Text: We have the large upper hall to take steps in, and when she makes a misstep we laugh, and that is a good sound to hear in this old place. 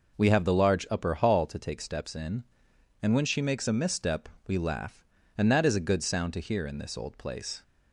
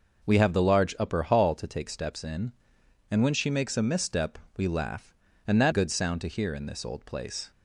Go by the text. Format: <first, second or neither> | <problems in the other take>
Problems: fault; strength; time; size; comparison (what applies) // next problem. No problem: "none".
first | pauses between "misstep" and "we"; slight; at 4.3 s; 0.18 s long; slight in the first // skips "is a"; at 5.7 s